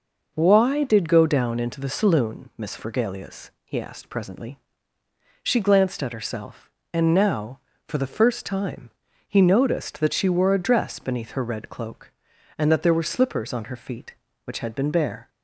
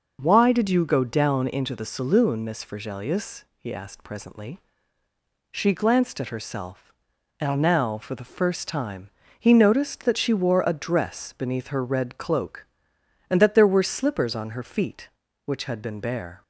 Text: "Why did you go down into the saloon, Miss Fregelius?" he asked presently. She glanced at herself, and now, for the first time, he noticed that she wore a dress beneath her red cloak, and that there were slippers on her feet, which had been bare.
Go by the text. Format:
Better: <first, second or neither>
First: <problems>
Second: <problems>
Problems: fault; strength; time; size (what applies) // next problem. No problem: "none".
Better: second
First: skips "you"; at 1.0 s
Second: none